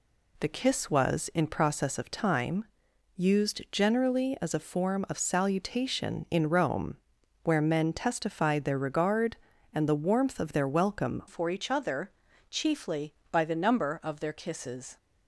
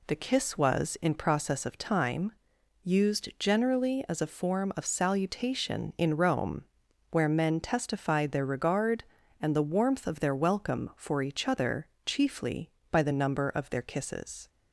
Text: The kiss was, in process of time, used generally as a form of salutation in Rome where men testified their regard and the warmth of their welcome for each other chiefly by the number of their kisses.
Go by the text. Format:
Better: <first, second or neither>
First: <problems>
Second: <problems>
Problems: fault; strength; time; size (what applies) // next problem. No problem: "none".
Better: second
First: pauses between "Rome" and "where"; noticeable; at 6.9 s; 0.48 s long // changes voice at "for"; from 11.2 s on; 3.7 s long // pauses between "other" and "chiefly"; at 12.1 s; 0.40 s long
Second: pauses between "Rome" and "where"; noticeable; at 6.6 s; 0.48 s long // pauses between "other" and "chiefly"; slight; at 11.8 s; 0.22 s long